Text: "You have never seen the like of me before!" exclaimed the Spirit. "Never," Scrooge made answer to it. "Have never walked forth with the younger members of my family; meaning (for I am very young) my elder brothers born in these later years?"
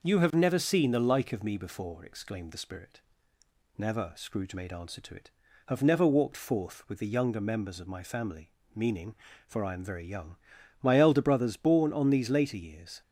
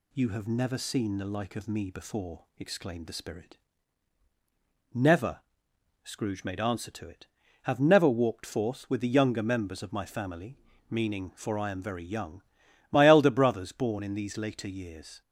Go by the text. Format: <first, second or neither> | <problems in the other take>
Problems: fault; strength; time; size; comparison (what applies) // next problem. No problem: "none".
second | says "on" for "in"; at 11.9 s